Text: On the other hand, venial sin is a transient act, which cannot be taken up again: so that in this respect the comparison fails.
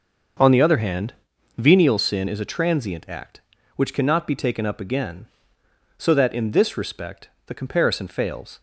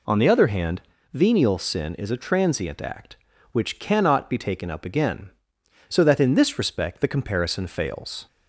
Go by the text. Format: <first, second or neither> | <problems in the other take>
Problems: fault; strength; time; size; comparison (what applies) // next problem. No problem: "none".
second | starts louder than the rest; until 1.8 s; 6.5 dB // pauses between "respect" and "the"; slight; at 7.3 s; 0.16 s long